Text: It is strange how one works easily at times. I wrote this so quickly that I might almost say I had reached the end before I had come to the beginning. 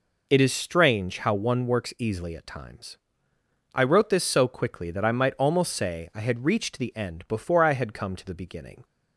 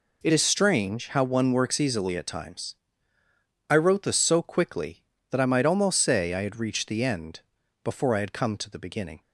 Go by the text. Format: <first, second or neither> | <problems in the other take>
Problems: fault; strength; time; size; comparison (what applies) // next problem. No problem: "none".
first | changes voice at "is"; from 0.3 s on; 8.8 s long // pauses between "end" and "before"; at 7.3 s; 0.44 s long